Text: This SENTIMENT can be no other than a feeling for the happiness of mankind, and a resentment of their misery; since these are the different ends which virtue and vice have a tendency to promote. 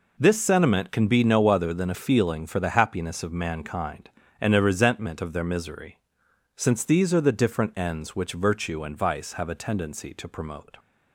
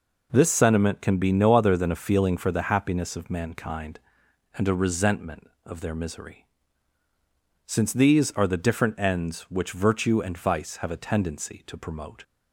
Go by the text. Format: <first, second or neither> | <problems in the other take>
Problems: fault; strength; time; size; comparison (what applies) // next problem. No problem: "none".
neither | none